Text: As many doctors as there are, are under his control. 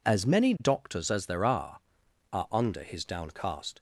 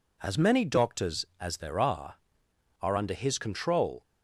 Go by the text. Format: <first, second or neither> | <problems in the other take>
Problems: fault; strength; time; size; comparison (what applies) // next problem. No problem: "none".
second | says "downcast" for "control"; at 3.0 s